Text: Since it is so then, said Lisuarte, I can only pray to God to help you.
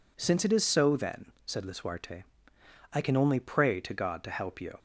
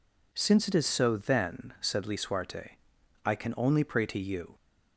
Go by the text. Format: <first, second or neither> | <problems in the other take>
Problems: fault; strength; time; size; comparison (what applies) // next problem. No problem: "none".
first | skips "God to help"; at 4.1 s